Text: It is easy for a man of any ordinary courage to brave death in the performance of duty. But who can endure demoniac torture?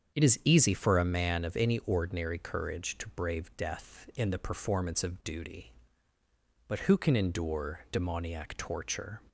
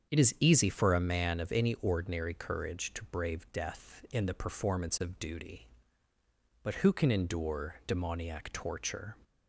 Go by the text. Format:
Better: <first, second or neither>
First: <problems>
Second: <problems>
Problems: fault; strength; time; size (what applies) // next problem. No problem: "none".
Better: neither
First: starts louder than the rest; strong; until 1.2 s; 7.5 dB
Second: starts louder than the rest; strong; until 1.1 s; 7.5 dB